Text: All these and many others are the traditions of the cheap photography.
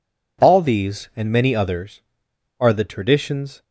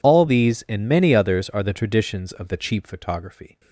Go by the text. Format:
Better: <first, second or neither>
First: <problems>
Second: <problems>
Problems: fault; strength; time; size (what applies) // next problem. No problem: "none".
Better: second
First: stops before "of the cheap photography"; at 3.6 s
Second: none